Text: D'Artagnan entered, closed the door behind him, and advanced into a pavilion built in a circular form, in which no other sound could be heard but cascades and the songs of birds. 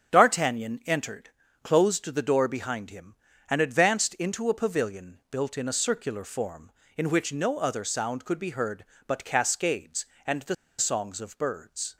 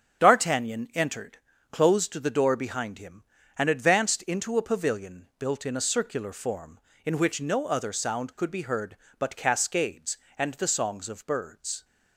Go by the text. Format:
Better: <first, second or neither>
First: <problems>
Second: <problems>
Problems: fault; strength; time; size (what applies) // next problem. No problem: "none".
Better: second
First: starts louder than the rest; strong; until 1.2 s; 8 dB // pauses between "the" and "songs"; slight; at 10.5 s; 0.24 s long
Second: starts louder than the rest; strong; until 1.2 s; 8 dB